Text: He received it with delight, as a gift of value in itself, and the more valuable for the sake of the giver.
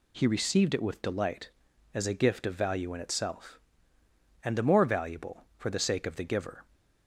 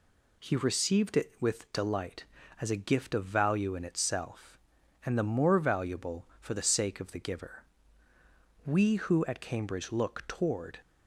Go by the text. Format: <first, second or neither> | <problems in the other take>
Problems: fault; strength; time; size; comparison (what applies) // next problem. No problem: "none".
first | goes on to say "We who at Cambridge look toward"; strong; from 8.6 s on; 2.1 s long